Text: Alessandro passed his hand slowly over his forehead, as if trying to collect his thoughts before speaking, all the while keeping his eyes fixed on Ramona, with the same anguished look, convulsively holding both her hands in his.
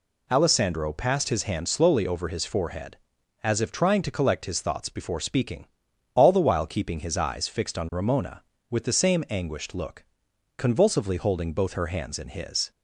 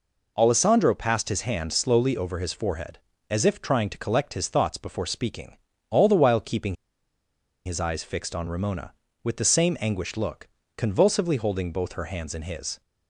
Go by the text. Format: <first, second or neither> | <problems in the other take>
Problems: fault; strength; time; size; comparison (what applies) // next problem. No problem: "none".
first | pauses between "keeping" and "his"; noticeable; at 6.7 s; 0.90 s long